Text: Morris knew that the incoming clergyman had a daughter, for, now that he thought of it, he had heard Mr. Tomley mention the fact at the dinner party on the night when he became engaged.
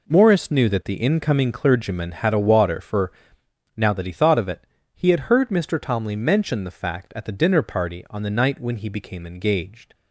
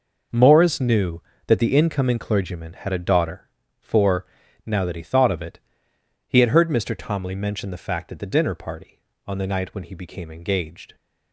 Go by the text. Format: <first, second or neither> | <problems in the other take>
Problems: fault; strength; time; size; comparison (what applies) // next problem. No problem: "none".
second | says "water" for "daughter"; at 2.3 s